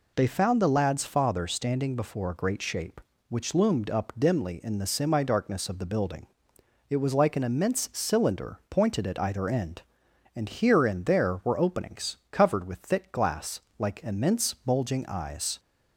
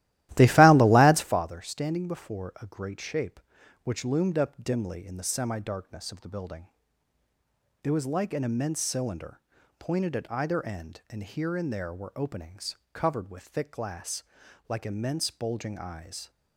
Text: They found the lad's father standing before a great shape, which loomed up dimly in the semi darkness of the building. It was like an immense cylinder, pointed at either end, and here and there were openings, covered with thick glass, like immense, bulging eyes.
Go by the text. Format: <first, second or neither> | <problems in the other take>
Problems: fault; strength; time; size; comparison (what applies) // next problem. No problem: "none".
first | starts louder than the rest; strong; until 1.4 s; 15 dB